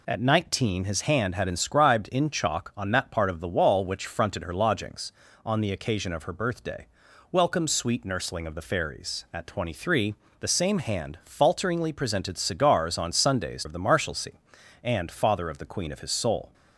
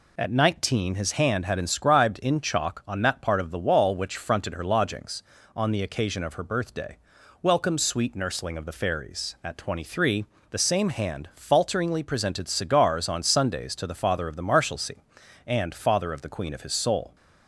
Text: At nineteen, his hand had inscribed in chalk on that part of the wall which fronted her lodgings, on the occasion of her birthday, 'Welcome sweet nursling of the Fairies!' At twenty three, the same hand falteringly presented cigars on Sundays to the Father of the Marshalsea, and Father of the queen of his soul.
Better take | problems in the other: second | skips "to the Father"; at 13.6 s

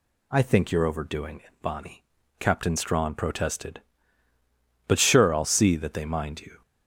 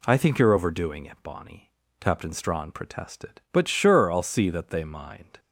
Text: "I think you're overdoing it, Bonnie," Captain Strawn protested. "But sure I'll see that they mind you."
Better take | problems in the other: first | stops before "you"; at 5.3 s

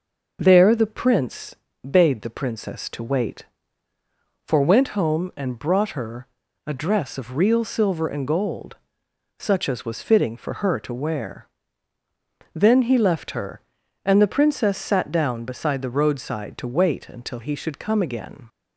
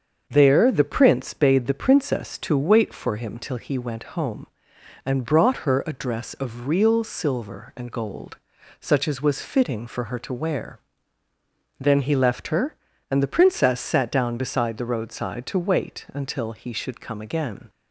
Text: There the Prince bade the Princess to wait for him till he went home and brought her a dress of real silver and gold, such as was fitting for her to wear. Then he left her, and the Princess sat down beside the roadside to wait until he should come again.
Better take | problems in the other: second | starts louder than the rest; noticeable; until 1.4 s; 6 dB; also in the second // pauses between "Prince" and "bade"; slight; at 1.5 s; 0.30 s long // skips "him till he"; at 4.6 s // pauses between "her" and "a"; at 6.2 s; 0.40 s long

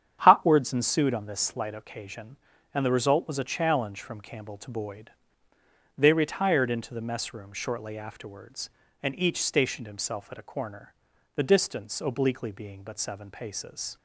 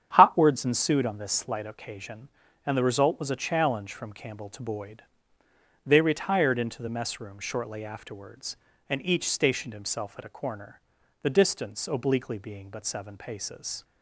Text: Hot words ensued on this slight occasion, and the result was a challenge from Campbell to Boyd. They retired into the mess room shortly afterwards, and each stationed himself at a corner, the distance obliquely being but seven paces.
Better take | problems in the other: neither | starts louder than the rest; strong; the same in both

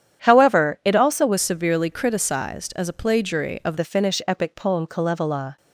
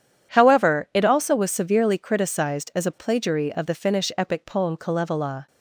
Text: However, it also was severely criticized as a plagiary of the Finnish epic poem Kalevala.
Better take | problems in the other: second | starts louder than the rest; strong; until 1.2 s; 9 dB // changes voice from "severely" to "of"; from 1.4 to 3.7 s; 2.3 s long

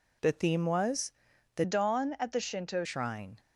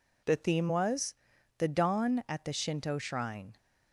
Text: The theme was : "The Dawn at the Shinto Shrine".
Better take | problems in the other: second | changes voice from "Dawn" to "Shinto"; from 1.6 to 2.8 s; 1.2 s long

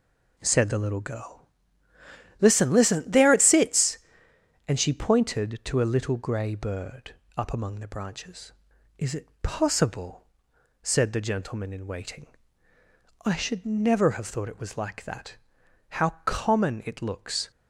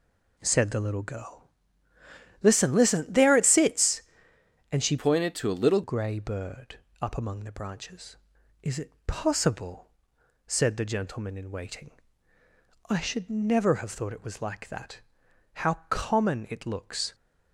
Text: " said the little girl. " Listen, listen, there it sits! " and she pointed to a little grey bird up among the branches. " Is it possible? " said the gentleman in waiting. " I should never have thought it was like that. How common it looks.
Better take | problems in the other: first | changes voice from "pointed" to "little"; from 4.9 to 5.8 s; 0.9 s long // pauses between "bird" and "up"; slight; at 6.7 s; 0.22 s long; slight in the first

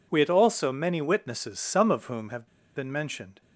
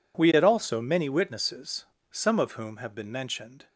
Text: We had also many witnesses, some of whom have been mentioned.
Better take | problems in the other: second | pauses between "have" and "been"; slight; at 2.4 s; 0.29 s long

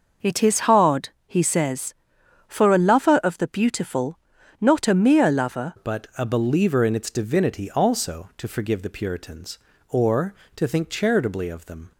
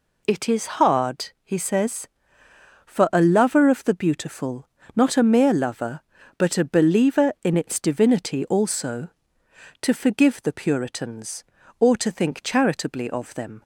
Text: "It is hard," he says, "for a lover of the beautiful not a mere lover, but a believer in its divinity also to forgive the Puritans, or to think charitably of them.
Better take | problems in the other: second | pauses between "beautiful" and "not"; at 4.1 s; 0.44 s long; slight in the second // changes voice at "but"; from 5.7 s on; 6.2 s long

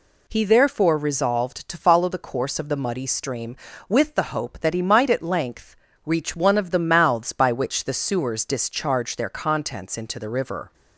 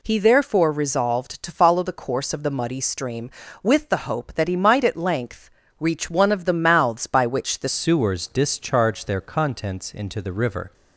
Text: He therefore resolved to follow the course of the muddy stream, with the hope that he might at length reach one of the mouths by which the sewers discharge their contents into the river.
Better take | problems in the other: first | pauses between "length" and "reach"; slight; at 5.4 s; 0.30 s long; slight in the first // changes voice at "sewers"; from 7.6 s on; 3.1 s long

